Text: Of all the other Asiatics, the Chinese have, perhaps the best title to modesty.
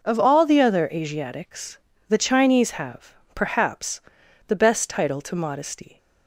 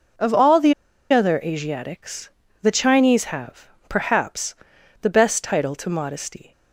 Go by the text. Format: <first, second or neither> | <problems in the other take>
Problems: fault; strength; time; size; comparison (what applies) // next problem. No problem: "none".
first | pauses between "the" and "other"; at 0.7 s; 0.37 s long // pauses between "perhaps" and "the"; noticeable; at 4.5 s; 0.48 s long; noticeable in the first